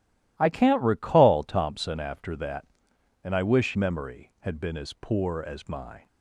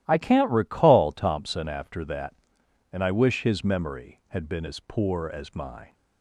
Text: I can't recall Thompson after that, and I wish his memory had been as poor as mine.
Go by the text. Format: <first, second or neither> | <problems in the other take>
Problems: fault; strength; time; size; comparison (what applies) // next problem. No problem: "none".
second | starts louder than the rest; strong; until 1.3 s; 15 dB; strong in the second // skips "his"; at 3.7 s